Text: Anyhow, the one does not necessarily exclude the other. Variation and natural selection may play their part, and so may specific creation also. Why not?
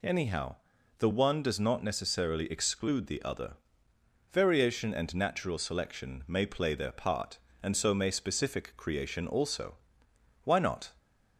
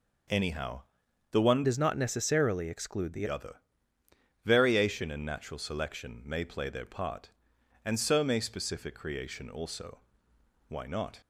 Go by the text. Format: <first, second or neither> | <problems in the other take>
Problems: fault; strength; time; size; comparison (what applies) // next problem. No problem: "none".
first | changes voice from "does" to "the"; from 1.6 to 3.2 s; 1.6 s long